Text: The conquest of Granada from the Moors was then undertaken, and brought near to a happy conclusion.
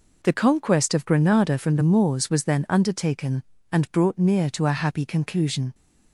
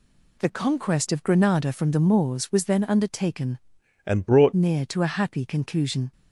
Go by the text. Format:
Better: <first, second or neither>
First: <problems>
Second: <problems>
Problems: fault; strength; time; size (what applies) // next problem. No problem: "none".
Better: first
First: none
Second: changes voice from "and" to "brought"; from 4.0 to 4.5 s; 0.5 s long